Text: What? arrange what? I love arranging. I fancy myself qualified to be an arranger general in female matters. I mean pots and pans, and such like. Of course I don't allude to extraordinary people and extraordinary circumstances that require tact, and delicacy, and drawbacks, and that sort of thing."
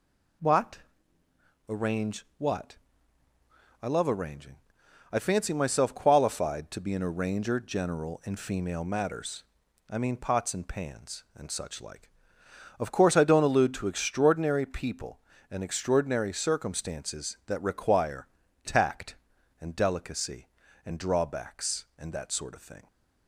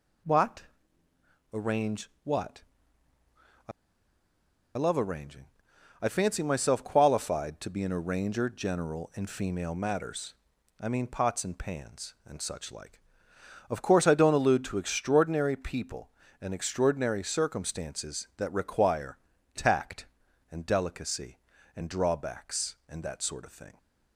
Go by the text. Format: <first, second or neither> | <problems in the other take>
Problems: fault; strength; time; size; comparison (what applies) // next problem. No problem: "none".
first | pauses between "I" and "love"; at 3.7 s; 1.0 s long // pauses between "require" and "tact"; slight; at 19.1 s; 0.36 s long; slight in the first